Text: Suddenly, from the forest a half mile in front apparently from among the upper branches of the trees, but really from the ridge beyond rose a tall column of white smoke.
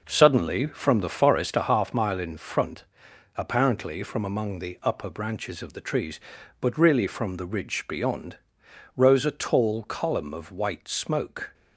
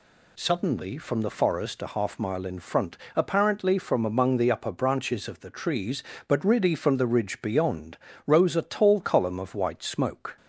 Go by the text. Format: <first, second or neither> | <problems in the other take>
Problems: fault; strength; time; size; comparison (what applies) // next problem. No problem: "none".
second | starts louder than the rest; noticeable; until 1.7 s; 5.5 dB // pauses between "front" and "apparently"; noticeable; at 2.8 s; 0.52 s long; slight in the second // pauses between "beyond" and "rose"; noticeable; at 8.3 s; 0.58 s long; slight in the second